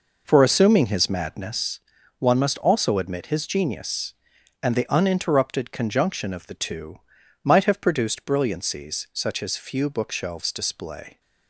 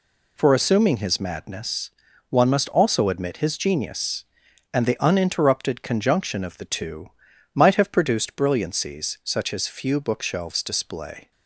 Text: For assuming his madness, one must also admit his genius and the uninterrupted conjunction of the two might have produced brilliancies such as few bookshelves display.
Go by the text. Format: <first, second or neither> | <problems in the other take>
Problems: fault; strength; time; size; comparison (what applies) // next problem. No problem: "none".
second | starts louder than the rest; noticeable; until 1.8 s; 5 dB // pauses between "two" and "might"; noticeable; at 6.9 s; 0.46 s long; noticeable in the second